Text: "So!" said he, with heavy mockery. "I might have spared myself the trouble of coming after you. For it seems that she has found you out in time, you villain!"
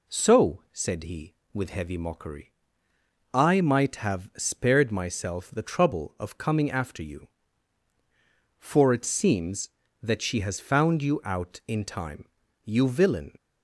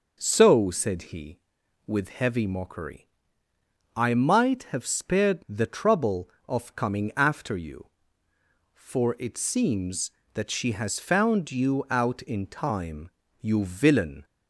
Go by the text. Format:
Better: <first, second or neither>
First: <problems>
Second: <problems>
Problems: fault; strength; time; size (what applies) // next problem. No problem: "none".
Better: first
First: none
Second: skips "myself"; at 5.4 s